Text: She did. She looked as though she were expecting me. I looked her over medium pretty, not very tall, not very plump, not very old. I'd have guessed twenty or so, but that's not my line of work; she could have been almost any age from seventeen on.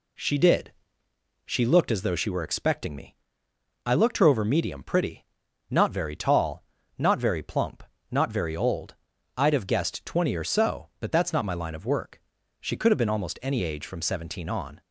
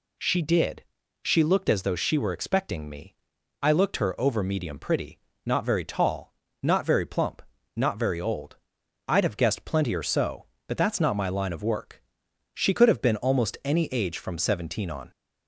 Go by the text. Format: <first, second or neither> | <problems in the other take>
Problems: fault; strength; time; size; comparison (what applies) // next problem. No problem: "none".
first | says "plenty" for "twenty"; at 9.6 s